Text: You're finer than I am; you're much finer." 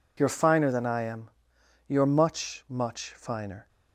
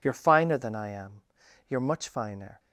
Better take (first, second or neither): second